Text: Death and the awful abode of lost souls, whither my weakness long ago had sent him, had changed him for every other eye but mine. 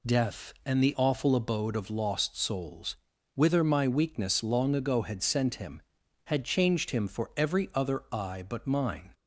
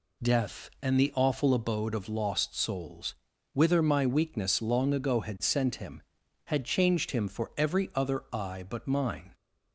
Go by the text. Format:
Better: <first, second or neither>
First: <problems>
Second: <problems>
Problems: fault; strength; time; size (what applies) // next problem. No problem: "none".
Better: neither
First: none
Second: none